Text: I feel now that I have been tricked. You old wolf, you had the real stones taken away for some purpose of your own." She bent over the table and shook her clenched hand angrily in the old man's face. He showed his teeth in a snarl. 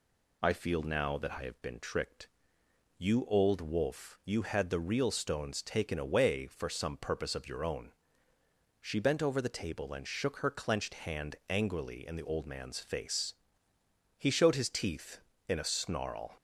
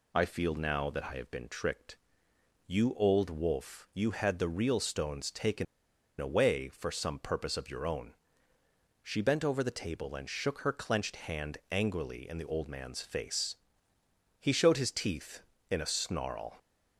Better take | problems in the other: first | pauses between "taken" and "away"; noticeable; at 5.6 s; 0.55 s long

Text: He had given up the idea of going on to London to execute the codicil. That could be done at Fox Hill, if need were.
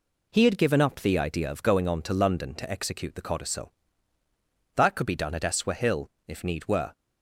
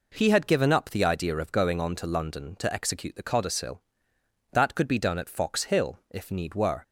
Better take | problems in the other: second | says "Eswa" for "Fox"; at 5.4 s

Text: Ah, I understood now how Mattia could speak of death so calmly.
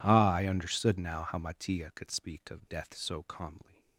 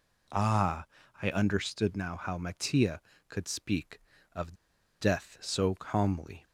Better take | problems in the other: first | pauses between "of" and "death"; noticeable; at 4.5 s; 0.47 s long

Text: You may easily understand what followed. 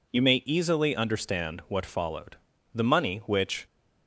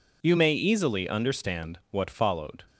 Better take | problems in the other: second | goes on to say "The money which"; noticeable; from 2.7 s on; 0.93 s long

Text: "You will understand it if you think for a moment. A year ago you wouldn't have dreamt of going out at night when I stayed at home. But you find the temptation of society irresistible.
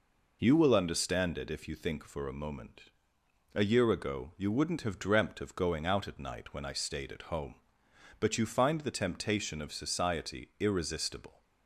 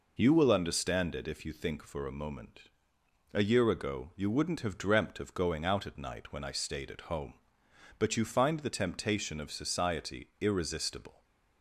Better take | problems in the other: neither | none

